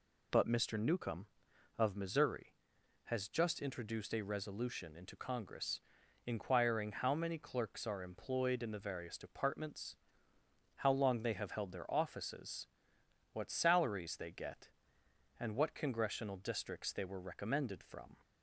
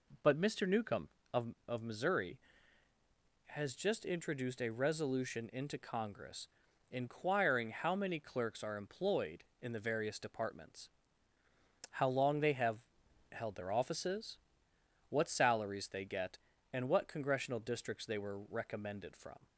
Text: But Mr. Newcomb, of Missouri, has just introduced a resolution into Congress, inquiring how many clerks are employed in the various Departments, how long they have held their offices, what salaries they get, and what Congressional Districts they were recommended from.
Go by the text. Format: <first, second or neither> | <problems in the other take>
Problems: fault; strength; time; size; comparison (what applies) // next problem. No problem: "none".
first | says "of" twice; at 1.6 s // pauses between "have" and "held"; noticeable; at 12.7 s; 0.54 s long